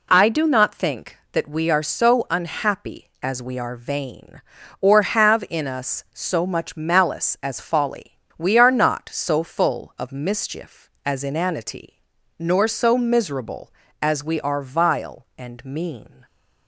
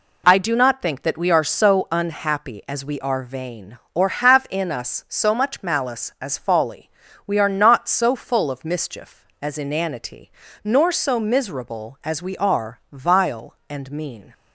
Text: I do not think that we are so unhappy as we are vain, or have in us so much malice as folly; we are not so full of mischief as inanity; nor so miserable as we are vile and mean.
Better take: neither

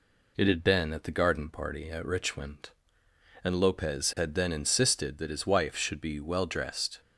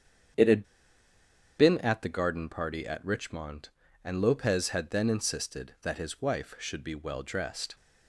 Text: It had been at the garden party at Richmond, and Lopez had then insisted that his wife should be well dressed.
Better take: first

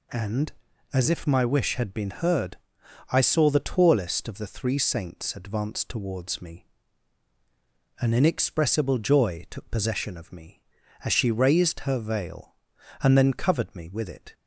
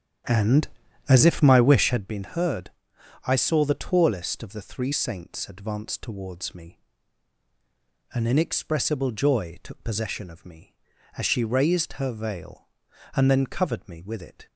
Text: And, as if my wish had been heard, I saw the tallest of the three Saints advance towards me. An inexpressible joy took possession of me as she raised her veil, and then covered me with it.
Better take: first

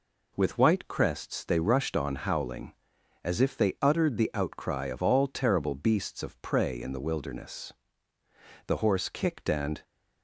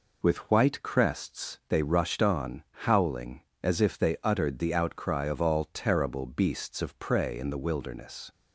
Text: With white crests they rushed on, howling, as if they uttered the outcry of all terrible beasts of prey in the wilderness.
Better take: second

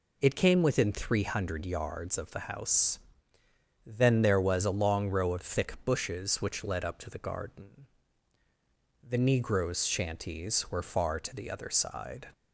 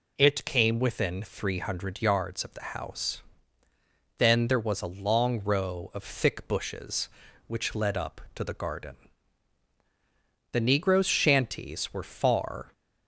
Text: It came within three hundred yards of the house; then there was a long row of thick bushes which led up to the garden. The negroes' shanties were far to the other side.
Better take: first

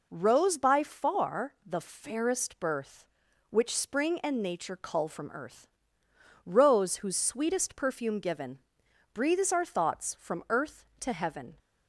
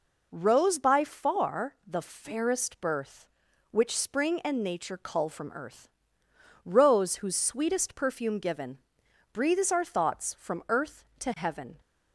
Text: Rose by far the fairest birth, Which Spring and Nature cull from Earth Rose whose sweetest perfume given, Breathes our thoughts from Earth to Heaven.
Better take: neither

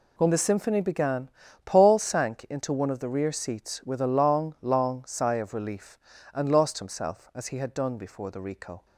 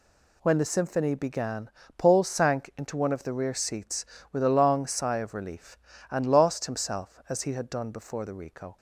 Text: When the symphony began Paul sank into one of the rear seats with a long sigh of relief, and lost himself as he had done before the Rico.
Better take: second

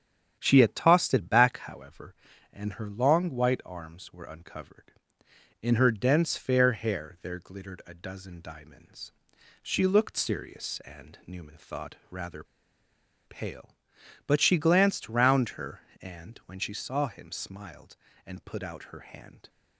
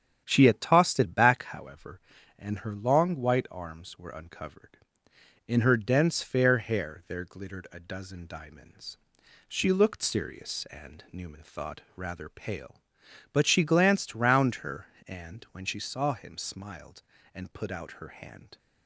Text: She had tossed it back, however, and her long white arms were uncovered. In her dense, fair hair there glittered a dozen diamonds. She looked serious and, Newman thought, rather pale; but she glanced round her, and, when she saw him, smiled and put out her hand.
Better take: second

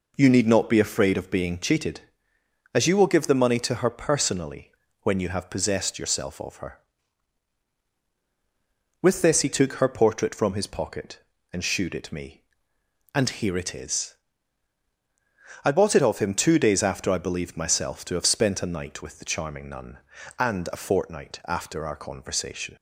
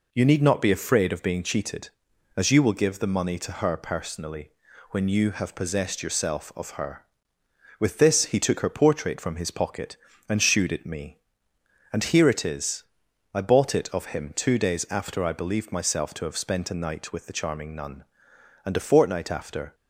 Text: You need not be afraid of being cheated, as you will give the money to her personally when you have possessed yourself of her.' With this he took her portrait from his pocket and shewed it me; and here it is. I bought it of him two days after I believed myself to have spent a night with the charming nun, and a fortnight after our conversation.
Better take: first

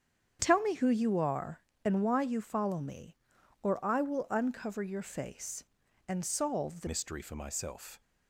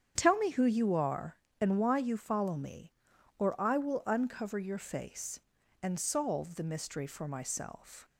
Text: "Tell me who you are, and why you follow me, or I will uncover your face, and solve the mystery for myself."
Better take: second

